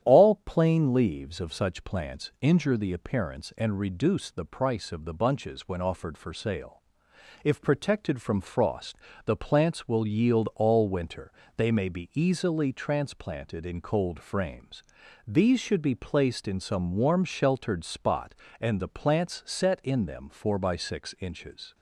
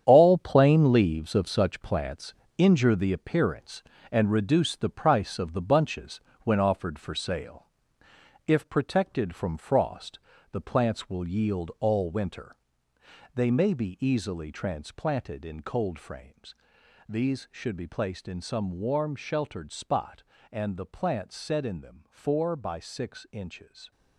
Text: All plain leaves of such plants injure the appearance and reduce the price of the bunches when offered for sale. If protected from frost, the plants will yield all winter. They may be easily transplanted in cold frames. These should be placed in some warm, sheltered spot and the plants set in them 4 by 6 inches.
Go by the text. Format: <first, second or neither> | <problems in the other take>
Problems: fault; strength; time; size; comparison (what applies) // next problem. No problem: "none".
first | gets quieter; strong; throughout; 10 dB // starts louder than the rest; strong; until 1.0 s; 9 dB; strong in the first // pauses between "plants" and "injure"; slight; at 2.3 s; 0.24 s long // pauses between "bunches" and "when"; slight; at 6.2 s; 0.22 s long